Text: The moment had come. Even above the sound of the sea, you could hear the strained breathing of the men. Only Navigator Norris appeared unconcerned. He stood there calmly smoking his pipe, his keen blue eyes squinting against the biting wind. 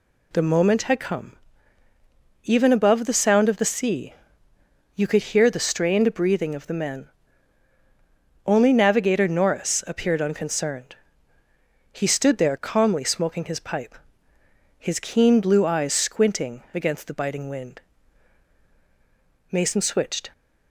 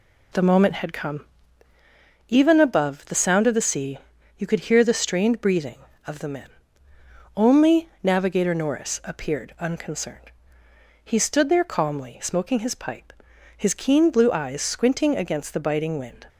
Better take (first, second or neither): second